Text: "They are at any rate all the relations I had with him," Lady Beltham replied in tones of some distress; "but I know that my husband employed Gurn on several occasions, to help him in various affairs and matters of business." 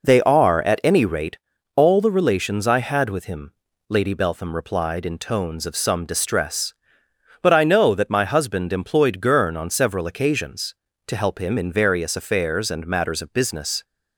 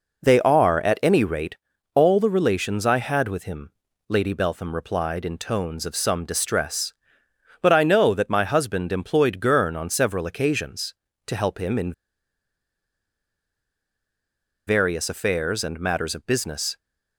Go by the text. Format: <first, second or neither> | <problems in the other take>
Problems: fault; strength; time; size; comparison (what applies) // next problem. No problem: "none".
first | pauses between "rate" and "all"; slight; at 1.5 s; 0.36 s long; slight in the first // pauses between "in" and "various"; strong; at 11.9 s; 2.7 s long